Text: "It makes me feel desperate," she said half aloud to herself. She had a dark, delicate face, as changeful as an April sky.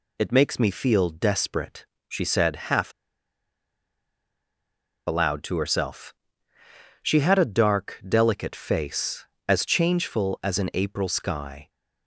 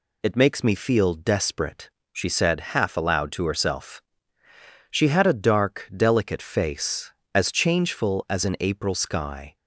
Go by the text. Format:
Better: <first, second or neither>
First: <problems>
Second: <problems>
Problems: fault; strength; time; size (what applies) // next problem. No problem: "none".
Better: second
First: pauses between "half" and "aloud"; strong; at 2.9 s; 2.1 s long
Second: none